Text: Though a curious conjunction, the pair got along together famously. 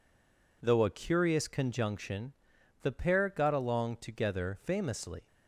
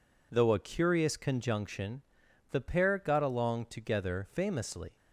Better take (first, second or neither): second